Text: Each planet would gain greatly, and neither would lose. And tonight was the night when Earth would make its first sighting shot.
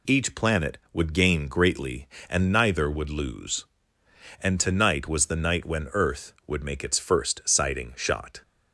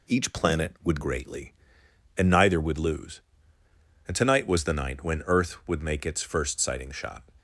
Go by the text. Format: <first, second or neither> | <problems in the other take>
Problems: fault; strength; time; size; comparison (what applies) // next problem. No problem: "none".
first | skips "gain"; at 1.0 s